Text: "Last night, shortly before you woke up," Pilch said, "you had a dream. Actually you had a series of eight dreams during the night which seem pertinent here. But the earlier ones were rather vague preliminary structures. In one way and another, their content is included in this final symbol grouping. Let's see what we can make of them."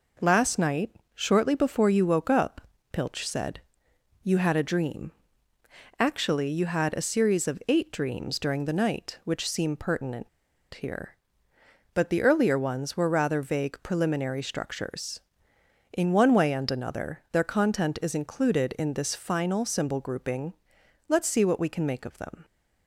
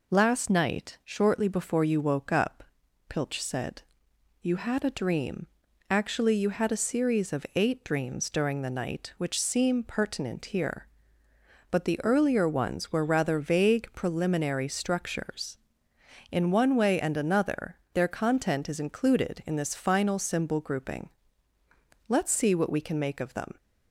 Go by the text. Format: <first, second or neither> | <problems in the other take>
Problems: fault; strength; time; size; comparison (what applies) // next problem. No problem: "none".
second | pauses between "pertinent" and "here"; at 10.2 s; 0.45 s long